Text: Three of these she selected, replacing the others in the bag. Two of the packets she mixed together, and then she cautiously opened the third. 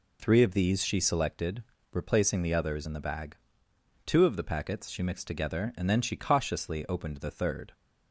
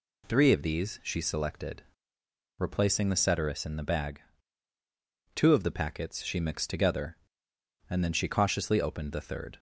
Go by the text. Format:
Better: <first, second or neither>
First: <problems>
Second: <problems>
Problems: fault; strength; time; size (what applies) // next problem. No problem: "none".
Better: first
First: none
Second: says "ceteris" for "others"; at 3.1 s